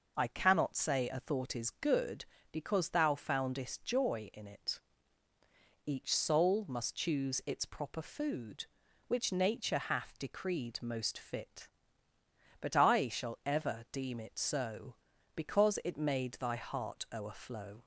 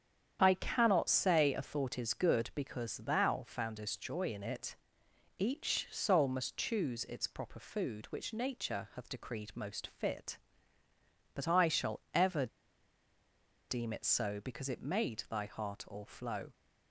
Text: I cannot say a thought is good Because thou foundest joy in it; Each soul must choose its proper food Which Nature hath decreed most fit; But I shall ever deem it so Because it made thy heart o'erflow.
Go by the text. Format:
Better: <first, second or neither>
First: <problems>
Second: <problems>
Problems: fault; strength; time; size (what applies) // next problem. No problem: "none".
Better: first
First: none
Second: starts louder than the rest; strong; until 1.4 s; 8 dB // pauses between "ever" and "deem"; at 12.4 s; 1.2 s long